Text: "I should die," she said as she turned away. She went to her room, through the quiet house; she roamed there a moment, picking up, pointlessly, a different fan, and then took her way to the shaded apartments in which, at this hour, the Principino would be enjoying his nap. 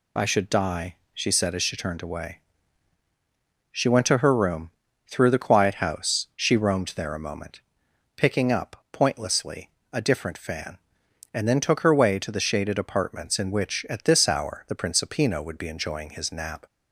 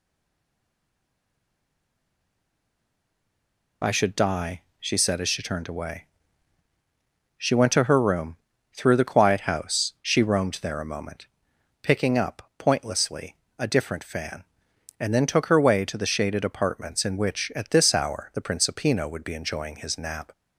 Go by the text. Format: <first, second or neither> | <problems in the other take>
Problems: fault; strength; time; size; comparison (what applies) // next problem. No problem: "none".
first | stays silent before the first word; strong; until 3.8 s; 3.8 s long